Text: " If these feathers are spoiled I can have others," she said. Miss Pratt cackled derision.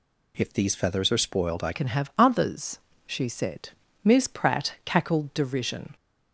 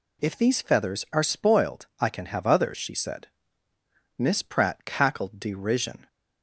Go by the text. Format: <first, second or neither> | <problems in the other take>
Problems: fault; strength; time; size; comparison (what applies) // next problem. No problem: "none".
second | changes voice at "can"; from 1.7 s on; 4.2 s long